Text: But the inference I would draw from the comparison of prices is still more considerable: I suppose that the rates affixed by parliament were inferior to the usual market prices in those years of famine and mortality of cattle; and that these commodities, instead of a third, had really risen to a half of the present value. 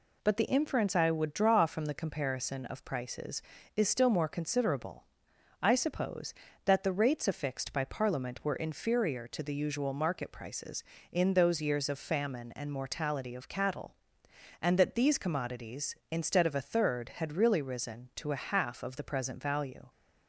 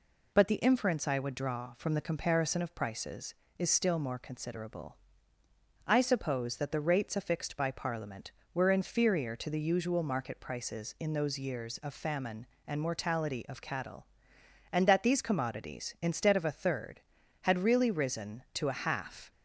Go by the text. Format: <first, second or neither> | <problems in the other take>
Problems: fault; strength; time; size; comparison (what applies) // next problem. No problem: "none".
first | stops before "of the present value"; at 19.3 s